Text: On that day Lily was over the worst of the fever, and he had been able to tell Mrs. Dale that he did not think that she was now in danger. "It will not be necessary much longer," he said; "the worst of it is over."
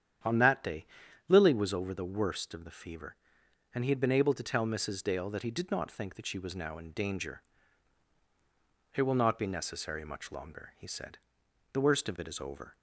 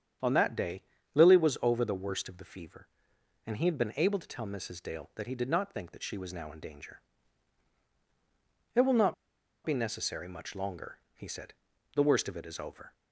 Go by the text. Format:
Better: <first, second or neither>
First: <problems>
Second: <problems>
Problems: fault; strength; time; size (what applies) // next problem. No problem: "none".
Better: first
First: starts louder than the rest; strong; until 1.6 s; 9 dB // pauses between "day" and "Lily"; at 0.8 s; 0.42 s long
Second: starts louder than the rest; strong; until 1.5 s; 8.5 dB // pauses between "day" and "Lily"; slight; at 0.8 s; 0.32 s long // pauses between "not" and "be"; noticeable; at 9.1 s; 0.50 s long